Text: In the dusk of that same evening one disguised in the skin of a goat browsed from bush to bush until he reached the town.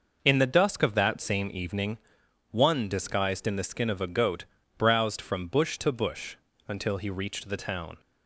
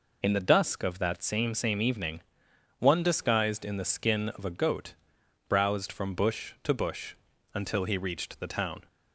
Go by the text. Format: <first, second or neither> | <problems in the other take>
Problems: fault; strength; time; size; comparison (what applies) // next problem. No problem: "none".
first | says "same" twice; at 1.5 s // pauses between "evening" and "one"; noticeable; at 2.2 s; 0.58 s long; noticeable in the first // pauses between "goat" and "browsed"; noticeable; at 4.9 s; 0.52 s long; slight in the first // pauses between "bush" and "until"; at 7.1 s; 0.38 s long; slight in the first